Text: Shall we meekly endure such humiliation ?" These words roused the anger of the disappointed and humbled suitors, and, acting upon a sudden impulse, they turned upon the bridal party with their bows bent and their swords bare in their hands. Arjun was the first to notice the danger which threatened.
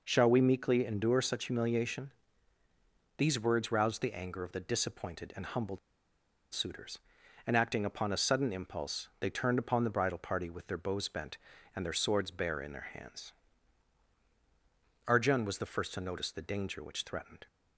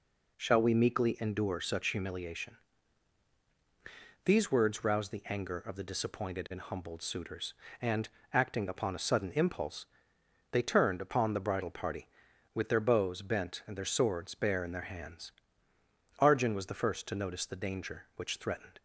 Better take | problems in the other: second | pauses between "humbled" and "suitors"; noticeable; at 5.7 s; 0.73 s long

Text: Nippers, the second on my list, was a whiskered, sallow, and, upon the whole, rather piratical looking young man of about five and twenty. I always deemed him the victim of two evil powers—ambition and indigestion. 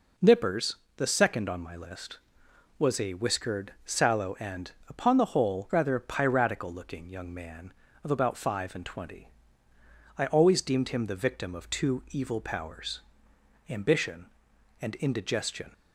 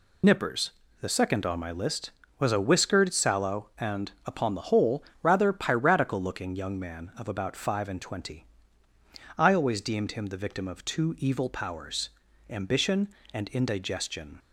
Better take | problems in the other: first | loses the start of "Nippers"; at 0.2 s; 50 ms

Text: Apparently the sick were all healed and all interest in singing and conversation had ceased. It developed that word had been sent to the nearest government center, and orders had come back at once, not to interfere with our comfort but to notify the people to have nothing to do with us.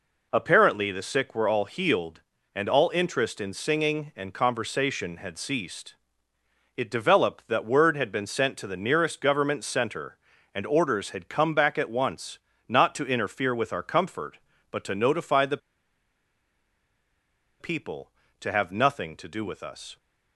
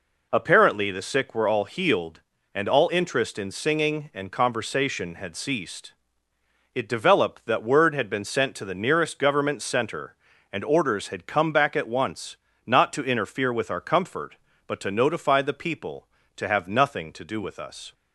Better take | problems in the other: second | pauses between "the" and "people"; strong; at 15.5 s; 2.0 s long

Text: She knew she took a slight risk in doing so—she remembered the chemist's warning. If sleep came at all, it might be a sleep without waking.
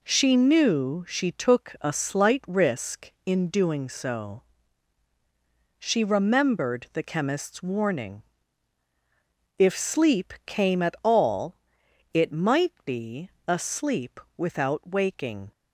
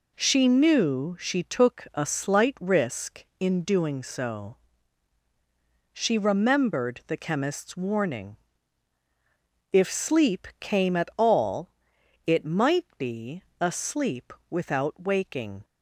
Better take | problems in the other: neither | pauses between "be" and "a"; slight; the same in both // pauses between "sleep" and "without"; slight; the same in both

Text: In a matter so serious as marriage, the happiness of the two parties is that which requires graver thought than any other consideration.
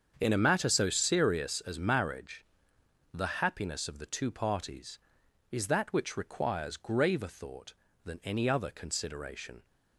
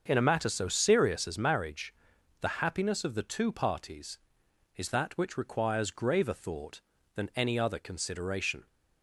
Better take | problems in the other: neither | starts louder than the rest; the same in both

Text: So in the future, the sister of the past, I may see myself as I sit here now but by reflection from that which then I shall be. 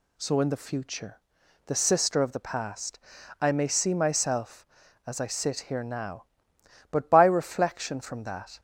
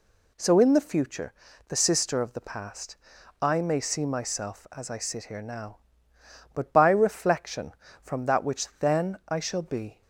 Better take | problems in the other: second | stops before "which then I shall be"; at 8.5 s

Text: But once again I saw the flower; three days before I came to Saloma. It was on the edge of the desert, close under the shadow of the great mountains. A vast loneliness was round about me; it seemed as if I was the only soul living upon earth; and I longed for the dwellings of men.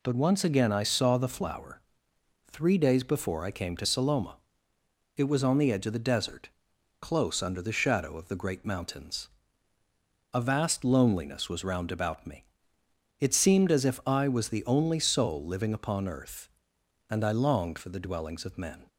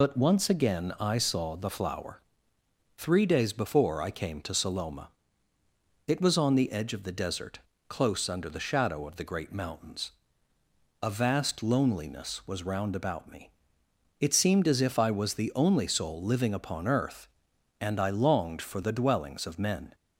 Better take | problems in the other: first | loses the start of "But"; at 0.0 s; 35 ms

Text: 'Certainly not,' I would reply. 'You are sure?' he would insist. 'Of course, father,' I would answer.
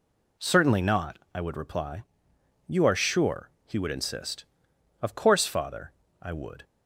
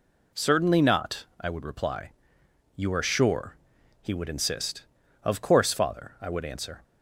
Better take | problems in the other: second | stops before "answer"; at 6.6 s

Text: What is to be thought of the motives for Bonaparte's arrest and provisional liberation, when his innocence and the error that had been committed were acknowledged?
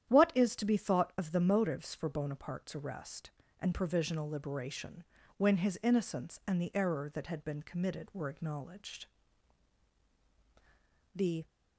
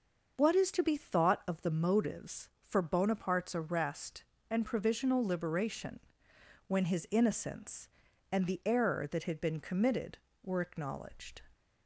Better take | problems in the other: second | starts louder than the rest; strong; until 1.1 s; 10 dB; noticeable in the second // goes on to say "The"; slight; from 11.1 s on; 0.32 s long

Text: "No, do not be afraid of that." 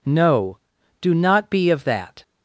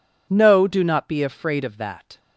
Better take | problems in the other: second | skips "afraid"; at 1.7 s

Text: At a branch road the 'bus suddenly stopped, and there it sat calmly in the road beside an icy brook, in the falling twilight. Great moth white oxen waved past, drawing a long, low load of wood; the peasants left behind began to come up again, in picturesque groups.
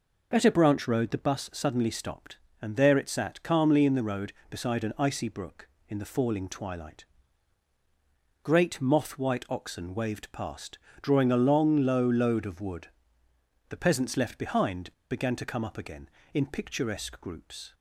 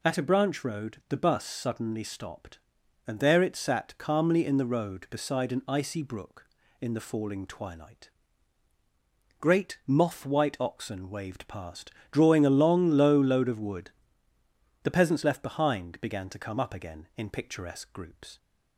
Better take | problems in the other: second | pauses between "behind" and "began"; slight; at 14.9 s; 0.20 s long

